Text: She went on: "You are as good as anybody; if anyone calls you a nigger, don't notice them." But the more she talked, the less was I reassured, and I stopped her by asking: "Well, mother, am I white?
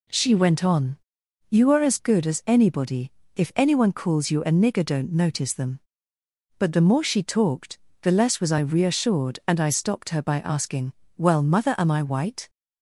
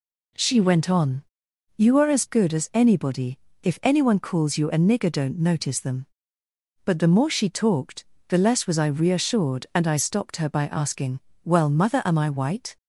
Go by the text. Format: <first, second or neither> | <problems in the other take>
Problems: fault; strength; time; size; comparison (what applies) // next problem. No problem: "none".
neither | none